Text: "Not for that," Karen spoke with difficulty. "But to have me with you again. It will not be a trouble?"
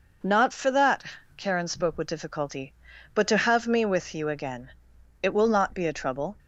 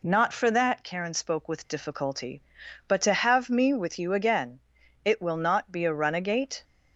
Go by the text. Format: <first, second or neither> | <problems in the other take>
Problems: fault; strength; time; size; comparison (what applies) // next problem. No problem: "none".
first | says "runagate" for "trouble"; at 5.9 s